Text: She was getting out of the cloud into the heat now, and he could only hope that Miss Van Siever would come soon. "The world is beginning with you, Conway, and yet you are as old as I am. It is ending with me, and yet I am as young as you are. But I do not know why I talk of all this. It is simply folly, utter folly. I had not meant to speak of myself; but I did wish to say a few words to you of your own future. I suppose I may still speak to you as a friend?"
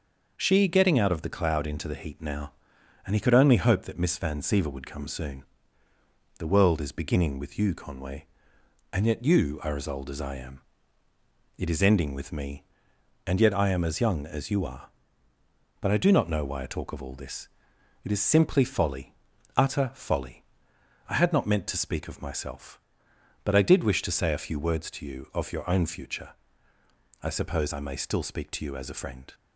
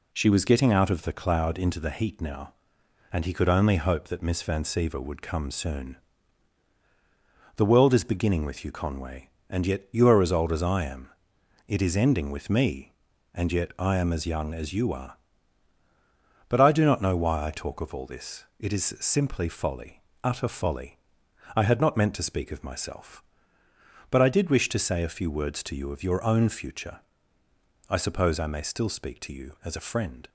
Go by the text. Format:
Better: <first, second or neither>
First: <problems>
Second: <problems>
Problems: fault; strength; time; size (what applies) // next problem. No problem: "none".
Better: second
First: skips "was"; at 0.6 s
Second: none